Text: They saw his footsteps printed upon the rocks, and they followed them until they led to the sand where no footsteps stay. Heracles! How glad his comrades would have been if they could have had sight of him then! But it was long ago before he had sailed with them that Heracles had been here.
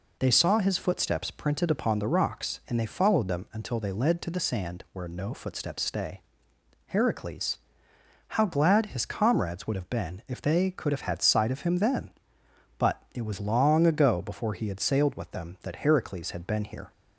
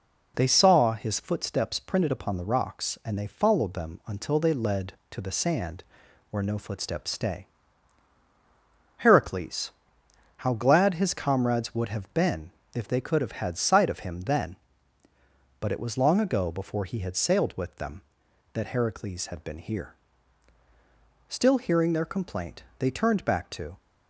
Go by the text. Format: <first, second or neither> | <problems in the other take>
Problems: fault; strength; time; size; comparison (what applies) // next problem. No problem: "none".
first | pauses between "sand" and "where"; noticeable; at 5.8 s; 0.46 s long // pauses between "been" and "if"; slight; at 12.5 s; 0.22 s long // goes on to say "Still hearing their complaint they turned back to"; strong; from 21.2 s on; 2.4 s long